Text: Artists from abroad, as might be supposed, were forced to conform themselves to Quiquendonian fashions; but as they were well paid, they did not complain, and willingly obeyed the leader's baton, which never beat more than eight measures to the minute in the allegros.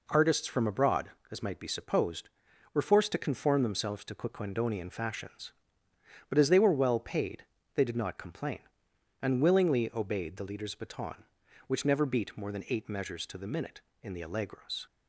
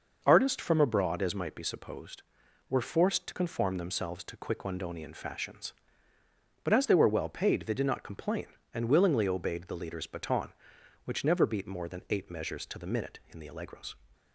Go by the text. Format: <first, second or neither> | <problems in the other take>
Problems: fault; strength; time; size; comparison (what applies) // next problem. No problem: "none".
neither | none